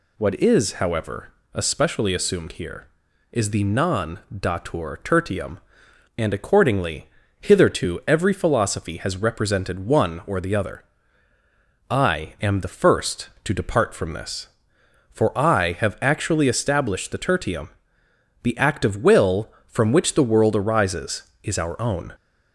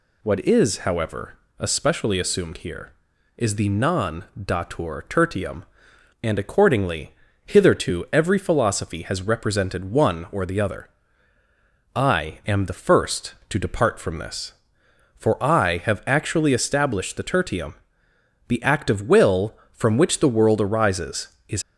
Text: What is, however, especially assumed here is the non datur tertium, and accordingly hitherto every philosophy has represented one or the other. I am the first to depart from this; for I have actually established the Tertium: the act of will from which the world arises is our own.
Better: first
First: pauses between "accordingly" and "hitherto"; slight; at 7.0 s; 0.34 s long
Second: pauses between "accordingly" and "hitherto"; slight; at 7.1 s; 0.34 s long // stops before "our own"; at 21.6 s

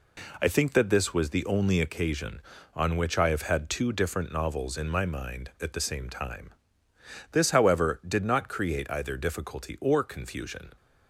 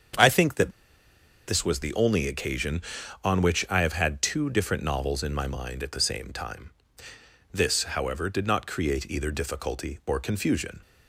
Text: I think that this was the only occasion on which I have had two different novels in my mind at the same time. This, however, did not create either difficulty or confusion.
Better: first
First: none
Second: starts louder than the rest; strong; until 1.9 s; 7.5 dB // pauses between "that" and "this"; noticeable; at 0.7 s; 0.77 s long

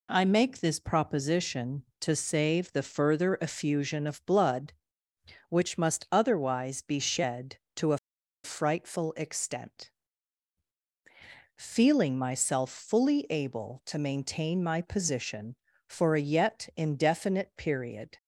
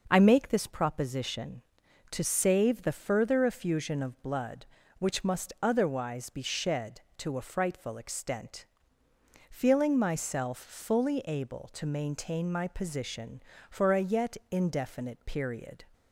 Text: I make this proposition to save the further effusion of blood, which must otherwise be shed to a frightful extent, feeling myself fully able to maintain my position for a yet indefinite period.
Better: second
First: pauses between "a" and "frightful"; noticeable; at 7.9 s; 0.46 s long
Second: none

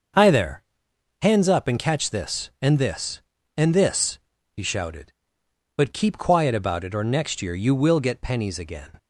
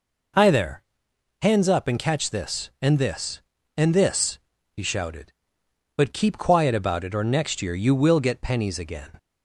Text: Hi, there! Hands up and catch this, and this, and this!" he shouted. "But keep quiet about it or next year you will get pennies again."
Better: second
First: gets quieter; throughout; 6.5 dB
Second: none

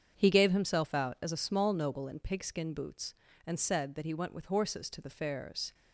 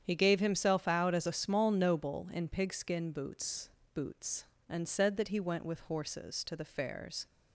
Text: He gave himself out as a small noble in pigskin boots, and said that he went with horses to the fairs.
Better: first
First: starts louder than the rest; strong; until 1.1 s; 7.5 dB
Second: starts louder than the rest; strong; until 1.0 s; 8.5 dB // says "boots" twice; at 3.9 s

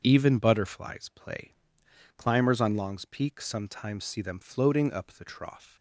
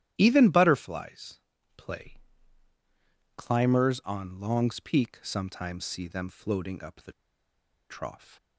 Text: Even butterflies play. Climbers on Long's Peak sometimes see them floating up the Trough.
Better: first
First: starts louder than the rest; until 1.0 s; 6.5 dB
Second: starts louder than the rest; strong; until 1.1 s; 12.5 dB // pauses between "butterflies" and "play"; at 1.3 s; 0.40 s long // pauses between "the" and "Trough"; noticeable; at 7.1 s; 0.77 s long

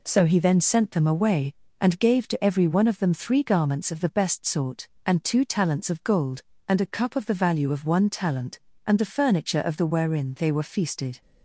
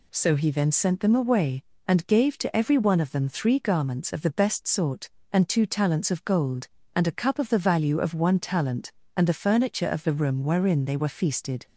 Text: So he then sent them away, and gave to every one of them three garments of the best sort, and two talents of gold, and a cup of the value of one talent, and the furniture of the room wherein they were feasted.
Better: second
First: skips "room"; at 9.8 s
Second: none

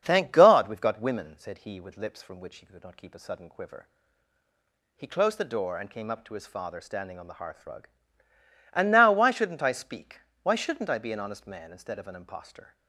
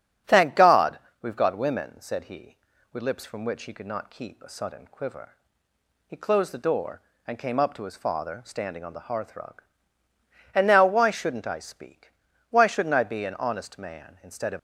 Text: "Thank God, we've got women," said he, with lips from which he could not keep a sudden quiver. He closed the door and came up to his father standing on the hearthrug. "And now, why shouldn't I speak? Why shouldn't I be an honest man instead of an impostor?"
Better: first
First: starts louder than the rest; strong; until 1.0 s; 7 dB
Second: starts louder than the rest; strong; until 1.4 s; 9 dB // stops before "an impostor"; at 14.5 s

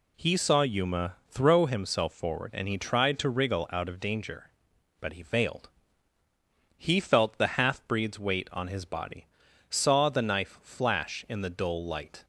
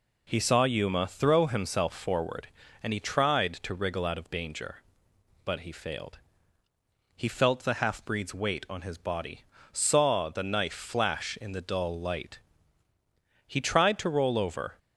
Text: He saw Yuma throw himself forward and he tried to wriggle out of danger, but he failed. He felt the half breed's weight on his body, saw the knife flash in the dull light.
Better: first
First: none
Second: goes on to say "He tried to roll over"; from 13.4 s on; 1.3 s long

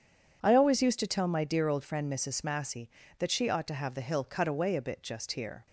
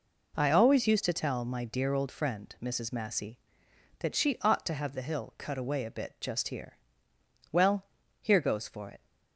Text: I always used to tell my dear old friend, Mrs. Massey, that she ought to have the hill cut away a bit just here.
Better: first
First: none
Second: goes on to say "Well here goes for it"; from 7.5 s on; 1.5 s long

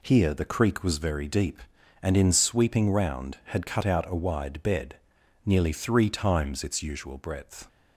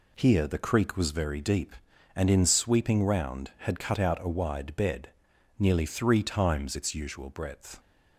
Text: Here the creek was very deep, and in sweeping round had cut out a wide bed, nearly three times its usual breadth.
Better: neither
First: none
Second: none

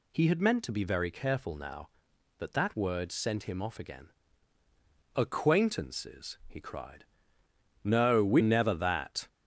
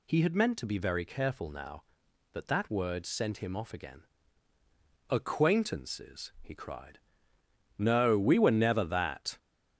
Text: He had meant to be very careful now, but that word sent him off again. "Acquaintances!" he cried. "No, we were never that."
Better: second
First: skips "were"; at 8.4 s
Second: none

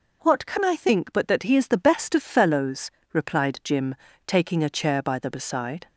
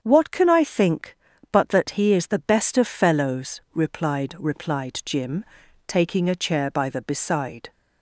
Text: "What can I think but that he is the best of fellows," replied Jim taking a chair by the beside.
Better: first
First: pauses between "Jim" and "taking"; slight; at 3.9 s; 0.30 s long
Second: starts louder than the rest; strong; until 1.0 s; 7.5 dB // says "replied" twice; at 4.3 s // pauses between "Jim" and "taking"; at 5.4 s; 0.44 s long

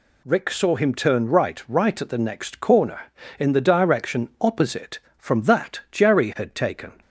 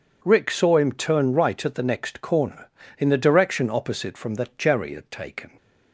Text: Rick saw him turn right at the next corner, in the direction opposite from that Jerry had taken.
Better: second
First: says "right" twice; at 1.6 s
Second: none

